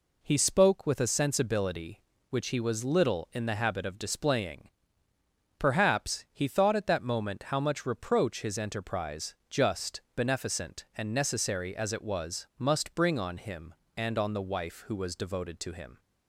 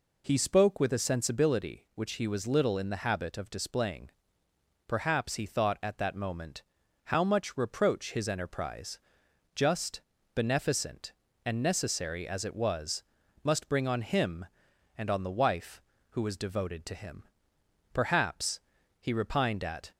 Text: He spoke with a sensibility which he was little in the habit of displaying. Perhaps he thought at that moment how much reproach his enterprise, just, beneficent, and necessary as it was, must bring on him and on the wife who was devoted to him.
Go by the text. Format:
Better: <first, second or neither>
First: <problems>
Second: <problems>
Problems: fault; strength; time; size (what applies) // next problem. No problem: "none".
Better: first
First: none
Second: pauses between "moment" and "how"; at 6.6 s; 0.40 s long // goes on to say "Perhaps he repined at"; strong; from 17.9 s on; 1.9 s long